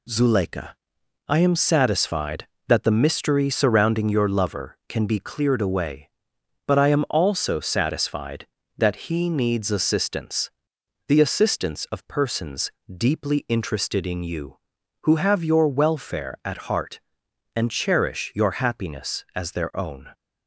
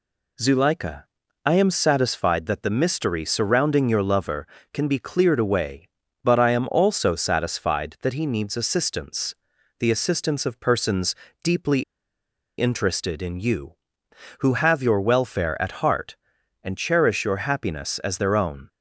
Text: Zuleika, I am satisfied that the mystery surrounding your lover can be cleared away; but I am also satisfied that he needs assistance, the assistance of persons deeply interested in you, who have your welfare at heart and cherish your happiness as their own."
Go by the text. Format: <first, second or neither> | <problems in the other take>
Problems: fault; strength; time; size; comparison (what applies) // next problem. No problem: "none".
first | pauses between "persons" and "deeply"; slight; at 11.1 s; 0.30 s long; slight in the first // pauses between "deeply" and "interested"; noticeable; at 11.8 s; 0.76 s long